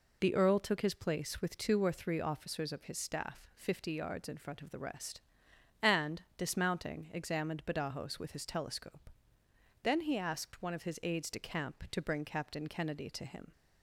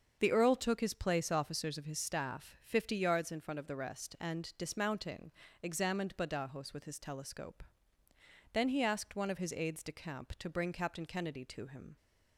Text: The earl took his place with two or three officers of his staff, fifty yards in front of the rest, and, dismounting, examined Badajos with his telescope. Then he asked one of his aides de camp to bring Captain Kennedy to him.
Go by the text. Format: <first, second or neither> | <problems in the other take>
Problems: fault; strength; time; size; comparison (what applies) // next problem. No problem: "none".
first | starts louder than the rest; until 1.2 s; 7 dB // skips "with two or three"; at 1.2 s